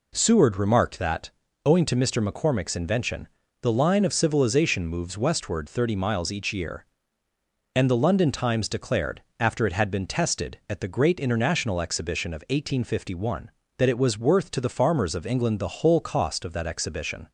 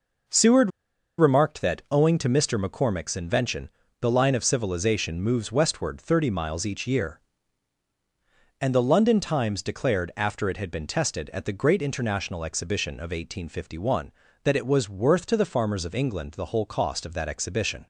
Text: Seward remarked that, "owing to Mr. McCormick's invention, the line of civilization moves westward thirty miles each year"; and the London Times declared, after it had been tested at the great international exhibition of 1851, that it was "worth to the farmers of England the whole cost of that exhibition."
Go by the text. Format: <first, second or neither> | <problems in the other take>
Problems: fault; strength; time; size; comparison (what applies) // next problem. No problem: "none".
first | pauses between "Seward" and "remarked"; noticeable; at 0.7 s; 0.47 s long